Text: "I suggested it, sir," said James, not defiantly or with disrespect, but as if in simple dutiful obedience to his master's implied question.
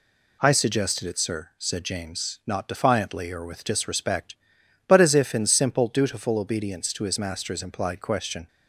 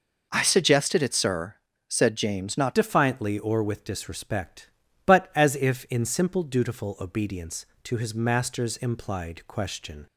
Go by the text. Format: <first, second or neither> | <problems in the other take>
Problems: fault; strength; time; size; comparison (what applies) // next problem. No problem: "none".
first | changes voice at "defiantly"; from 2.7 s on; 7.3 s long